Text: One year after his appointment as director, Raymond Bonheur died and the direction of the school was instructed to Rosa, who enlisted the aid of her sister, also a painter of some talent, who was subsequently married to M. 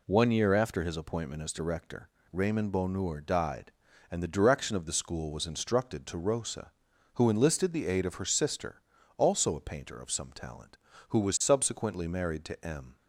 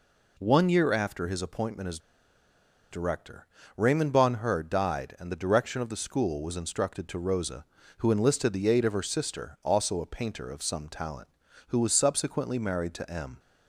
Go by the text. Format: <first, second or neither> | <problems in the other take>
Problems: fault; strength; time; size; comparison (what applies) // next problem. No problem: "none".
first | pauses between "as" and "director"; noticeable; at 1.9 s; 0.92 s long